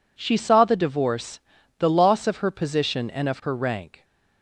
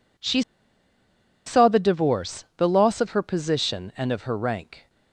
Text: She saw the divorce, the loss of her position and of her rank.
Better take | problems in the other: first | pauses between "She" and "saw"; at 0.4 s; 1.0 s long

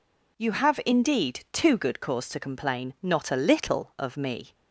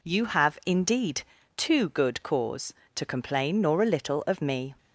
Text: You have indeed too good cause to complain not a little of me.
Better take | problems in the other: first | pauses between "indeed" and "too"; slight; at 1.2 s; 0.36 s long // says "nor" for "not"; at 3.6 s

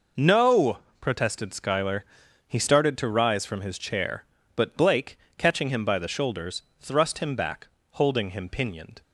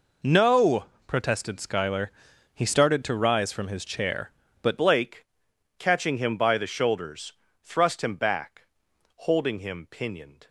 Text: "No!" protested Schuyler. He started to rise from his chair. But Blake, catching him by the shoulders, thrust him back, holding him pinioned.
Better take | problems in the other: first | changes voice at "Blake"; from 4.7 s on; 5.7 s long

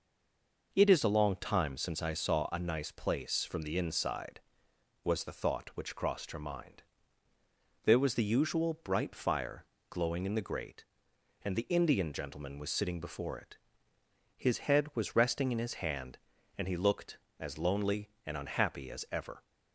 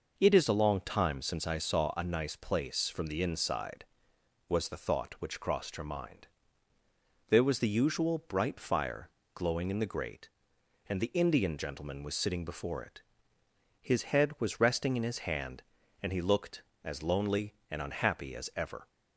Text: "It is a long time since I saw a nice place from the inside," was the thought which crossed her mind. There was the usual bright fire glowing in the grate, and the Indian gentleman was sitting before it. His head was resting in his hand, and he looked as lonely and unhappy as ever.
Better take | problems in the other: second | stays silent before the first word; slight; until 0.7 s; 0.7 s long // pauses between "fire" and "glowing"; slight; at 9.6 s; 0.24 s long; slight in the second

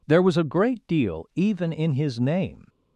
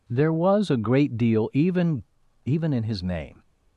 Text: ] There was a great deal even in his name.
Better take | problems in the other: first | says "even" twice; at 2.4 s

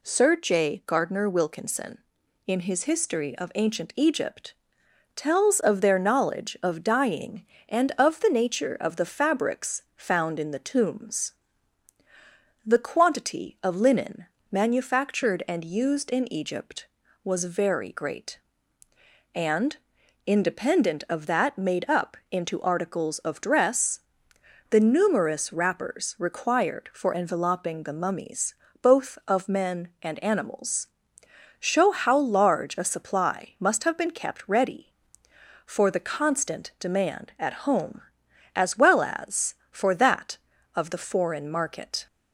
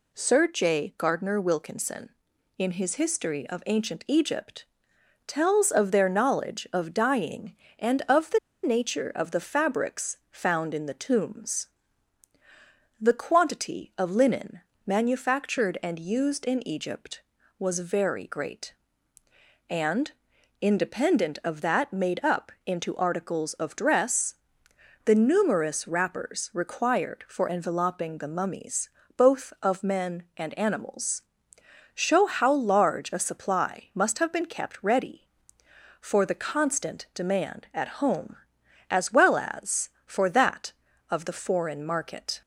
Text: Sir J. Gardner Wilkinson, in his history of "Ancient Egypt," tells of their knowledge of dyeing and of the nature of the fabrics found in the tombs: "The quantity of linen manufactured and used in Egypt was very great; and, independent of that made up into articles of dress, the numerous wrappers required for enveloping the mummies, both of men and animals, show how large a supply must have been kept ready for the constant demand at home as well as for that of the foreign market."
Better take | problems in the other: first | pauses between "the" and "nature"; slight; at 8.3 s; 0.24 s long // pauses between "linen" and "manufactured"; slight; at 14.6 s; 0.24 s long; slight in the first // pauses between "up" and "into"; slight; at 22.5 s; 0.16 s long; slight in the first

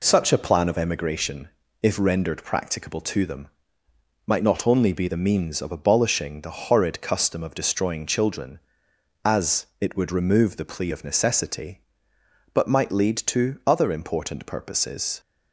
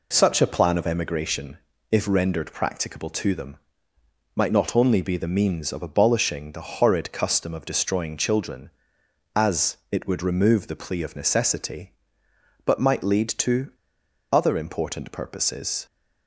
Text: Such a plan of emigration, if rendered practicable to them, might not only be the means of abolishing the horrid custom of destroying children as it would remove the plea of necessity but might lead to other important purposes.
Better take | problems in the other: first | pauses between "to" and "other"; noticeable; at 13.6 s; 0.61 s long

